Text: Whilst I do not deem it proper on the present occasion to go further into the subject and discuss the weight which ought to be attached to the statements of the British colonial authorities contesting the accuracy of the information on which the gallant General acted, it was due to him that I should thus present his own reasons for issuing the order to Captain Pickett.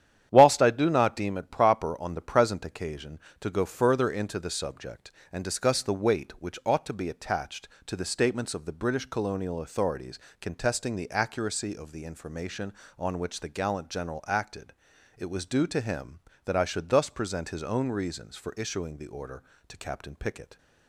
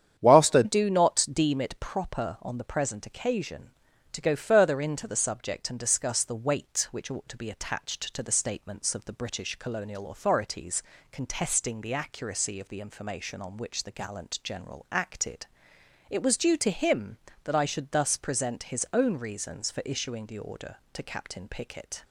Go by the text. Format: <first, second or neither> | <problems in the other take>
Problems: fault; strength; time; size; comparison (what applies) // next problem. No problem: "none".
first | starts louder than the rest; strong; until 1.2 s; 9 dB; strong in the first // changes voice at "do"; from 0.6 s on; 21.4 s long // pauses between "authorities" and "contesting"; slight; at 10.8 s; 0.28 s long; slight in the first